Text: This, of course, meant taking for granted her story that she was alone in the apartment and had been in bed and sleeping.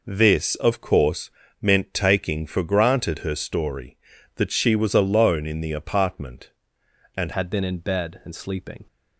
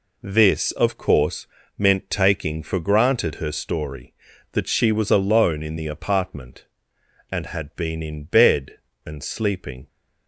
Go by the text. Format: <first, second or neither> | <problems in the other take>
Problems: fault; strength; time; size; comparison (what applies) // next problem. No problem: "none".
second | changes voice at "had"; from 7.3 s on; 1.5 s long